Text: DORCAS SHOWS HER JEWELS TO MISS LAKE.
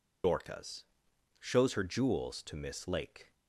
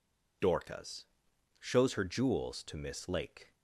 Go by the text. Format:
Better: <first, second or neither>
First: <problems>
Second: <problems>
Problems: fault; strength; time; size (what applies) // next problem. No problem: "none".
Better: second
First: loses the start of "DORCAS"; at 0.2 s; 60 ms // pauses between "DORCAS" and "SHOWS"; noticeable; at 0.8 s; 0.56 s long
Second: pauses between "DORCAS" and "SHOWS"; noticeable; at 1.0 s; 0.54 s long